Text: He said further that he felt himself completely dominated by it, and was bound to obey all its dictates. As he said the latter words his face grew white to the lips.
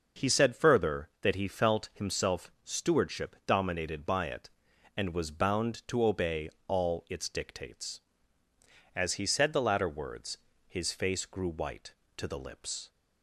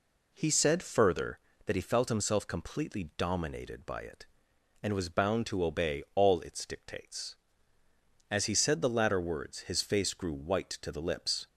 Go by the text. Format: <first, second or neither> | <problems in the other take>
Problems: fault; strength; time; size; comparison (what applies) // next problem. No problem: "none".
second | says "stewardship" for "completely"; at 2.6 s // pauses between "obey" and "all"; slight; at 6.4 s; 0.18 s long // pauses between "words" and "his"; slight; at 10.3 s; 0.28 s long